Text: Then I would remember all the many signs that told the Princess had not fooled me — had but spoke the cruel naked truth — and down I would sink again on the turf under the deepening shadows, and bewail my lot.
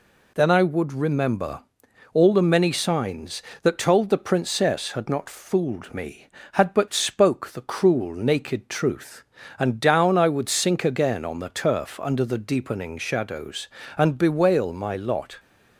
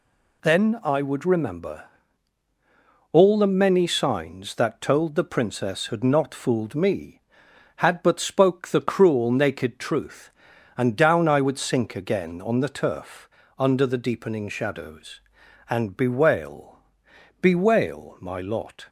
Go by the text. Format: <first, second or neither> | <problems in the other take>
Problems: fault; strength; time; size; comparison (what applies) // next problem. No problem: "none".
first | pauses between "remember" and "all"; strong; at 1.8 s; 1.2 s long; noticeable in the first // pauses between "turf" and "under"; slight; at 13.2 s; 0.30 s long // says "bewail" twice; at 17.4 s